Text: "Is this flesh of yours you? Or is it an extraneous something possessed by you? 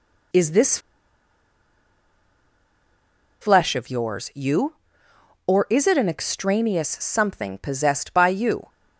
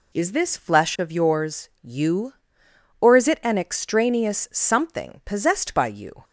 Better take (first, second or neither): second